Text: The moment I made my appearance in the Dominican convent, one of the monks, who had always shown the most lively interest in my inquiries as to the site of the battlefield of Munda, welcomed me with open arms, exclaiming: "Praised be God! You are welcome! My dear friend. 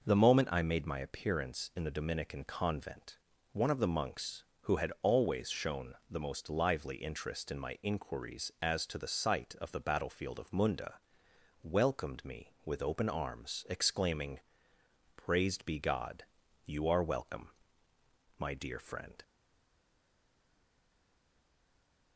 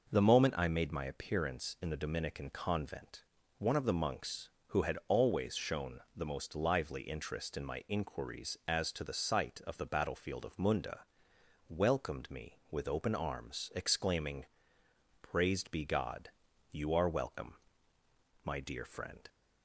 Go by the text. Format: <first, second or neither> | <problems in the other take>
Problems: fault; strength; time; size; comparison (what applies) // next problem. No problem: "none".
second | pauses between "shown" and "the"; slight; at 5.9 s; 0.16 s long; slight in the second // stays silent after the last word; strong; from 19.2 s on; 2.9 s long